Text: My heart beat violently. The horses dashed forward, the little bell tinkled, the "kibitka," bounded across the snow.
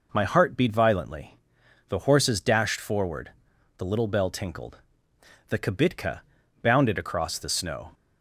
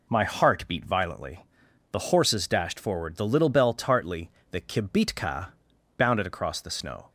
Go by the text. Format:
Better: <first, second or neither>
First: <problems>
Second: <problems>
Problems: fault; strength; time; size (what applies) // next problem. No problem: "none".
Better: first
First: none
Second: says "tartly" for "tinkled"; at 3.7 s